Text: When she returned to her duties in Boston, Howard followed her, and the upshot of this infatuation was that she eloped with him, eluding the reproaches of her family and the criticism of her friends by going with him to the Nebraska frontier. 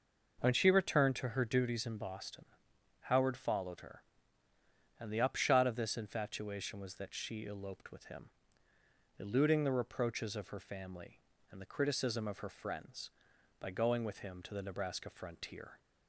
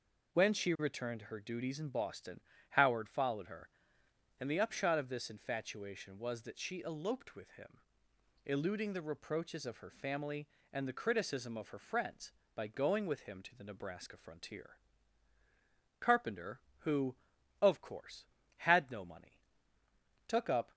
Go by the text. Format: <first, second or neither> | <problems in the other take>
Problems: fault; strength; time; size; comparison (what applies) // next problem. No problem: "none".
first | goes on to say "Carpenter who of course had no money took up"; strong; from 15.9 s on; 4.7 s long